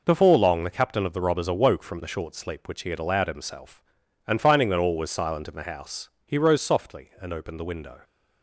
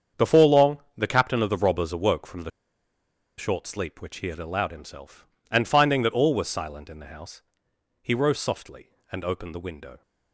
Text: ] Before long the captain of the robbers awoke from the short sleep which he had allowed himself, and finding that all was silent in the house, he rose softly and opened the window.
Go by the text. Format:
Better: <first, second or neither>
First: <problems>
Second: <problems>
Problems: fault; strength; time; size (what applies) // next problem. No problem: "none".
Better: first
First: none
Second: starts louder than the rest; strong; until 1.3 s; 7.5 dB // pauses between "long" and "the"; slight; at 0.7 s; 0.18 s long // pauses between "the" and "short"; noticeable; at 2.5 s; 0.89 s long